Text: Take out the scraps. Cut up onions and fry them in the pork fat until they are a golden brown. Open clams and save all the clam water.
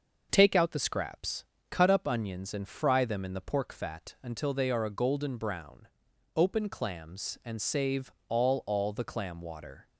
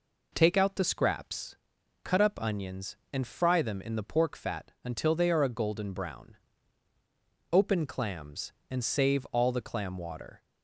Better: second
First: starts louder than the rest; until 1.3 s; 6 dB // pauses between "save" and "all"; slight; at 8.1 s; 0.16 s long // says "all" twice; at 8.6 s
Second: none

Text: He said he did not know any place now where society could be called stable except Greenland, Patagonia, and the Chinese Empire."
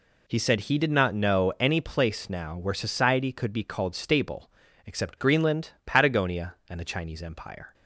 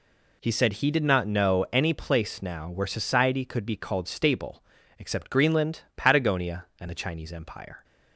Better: neither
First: pauses between "stable" and "except"; slight; at 4.4 s; 0.36 s long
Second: pauses between "stable" and "except"; slight; at 4.6 s; 0.36 s long

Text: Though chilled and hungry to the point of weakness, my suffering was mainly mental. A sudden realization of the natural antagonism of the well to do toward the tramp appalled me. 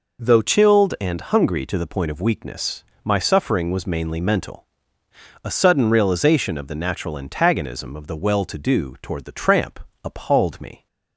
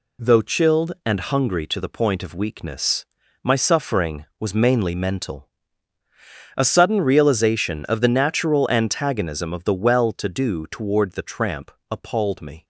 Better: second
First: changes voice at "chilled"; from 0.4 s on; 10.4 s long // pauses between "tramp" and "appalled"; slight; at 9.7 s; 0.24 s long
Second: pauses between "tramp" and "appalled"; slight; at 11.7 s; 0.18 s long

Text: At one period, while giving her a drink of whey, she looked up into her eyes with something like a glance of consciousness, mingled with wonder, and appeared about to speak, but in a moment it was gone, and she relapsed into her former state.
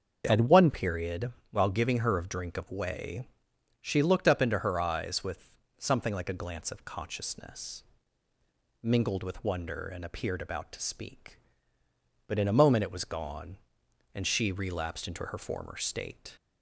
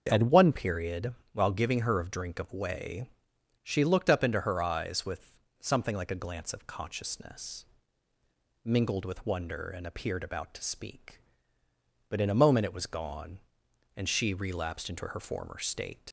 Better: first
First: starts louder than the rest; until 1.2 s; 6.5 dB // pauses between "with" and "something"; slight; at 5.5 s; 0.24 s long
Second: starts louder than the rest; until 1.1 s; 6.5 dB // pauses between "with" and "something"; slight; at 5.3 s; 0.24 s long // leaves "state" unfinished; at 16.0 s; 65 ms

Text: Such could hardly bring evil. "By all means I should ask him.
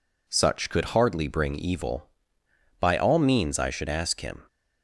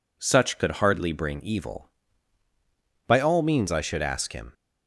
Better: neither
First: none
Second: none

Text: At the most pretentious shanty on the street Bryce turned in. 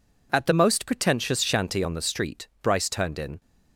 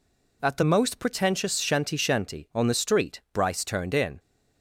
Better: first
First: none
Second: says "shanty" twice; at 1.9 s

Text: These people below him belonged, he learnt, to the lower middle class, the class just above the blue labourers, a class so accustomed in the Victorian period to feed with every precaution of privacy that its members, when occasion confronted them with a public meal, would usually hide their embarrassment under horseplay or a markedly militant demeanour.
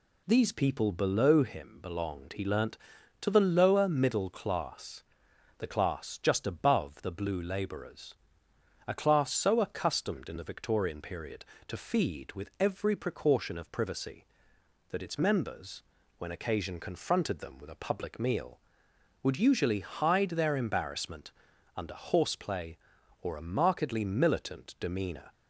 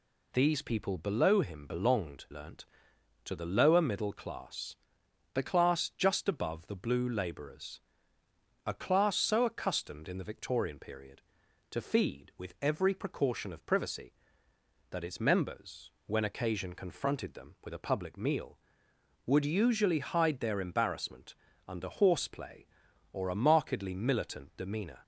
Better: first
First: pauses between "embarrassment" and "under"; at 21.3 s; 0.42 s long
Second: skips "he"; at 2.2 s // pauses between "embarrassment" and "under"; slight; at 21.3 s; 0.32 s long

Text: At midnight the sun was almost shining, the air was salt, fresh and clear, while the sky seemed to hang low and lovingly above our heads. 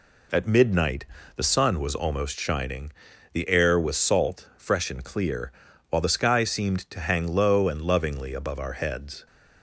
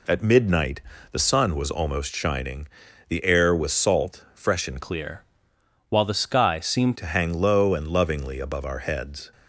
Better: first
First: pauses between "midnight" and "the"; slight; at 1.0 s; 0.30 s long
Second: pauses between "midnight" and "the"; slight; at 0.8 s; 0.30 s long // changes voice from "clear" to "seemed"; from 4.7 to 6.9 s; 2.2 s long

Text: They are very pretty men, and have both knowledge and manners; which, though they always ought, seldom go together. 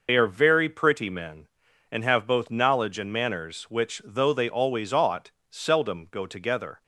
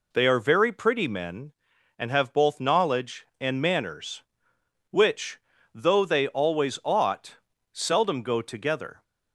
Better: second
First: loses the start of "They"; at 0.0 s; 60 ms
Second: none

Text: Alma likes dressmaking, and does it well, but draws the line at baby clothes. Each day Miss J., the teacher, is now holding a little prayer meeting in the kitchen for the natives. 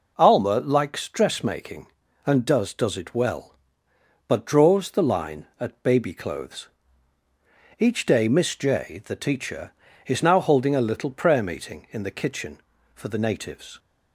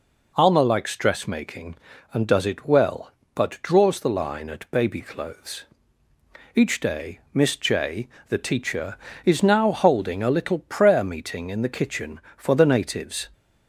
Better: second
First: says "does" twice; at 2.7 s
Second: none

